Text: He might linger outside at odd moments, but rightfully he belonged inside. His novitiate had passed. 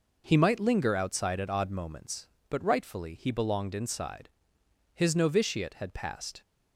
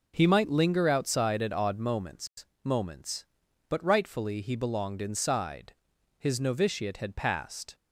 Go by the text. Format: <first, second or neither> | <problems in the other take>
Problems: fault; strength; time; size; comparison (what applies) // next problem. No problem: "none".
first | says "moments" twice; at 2.6 s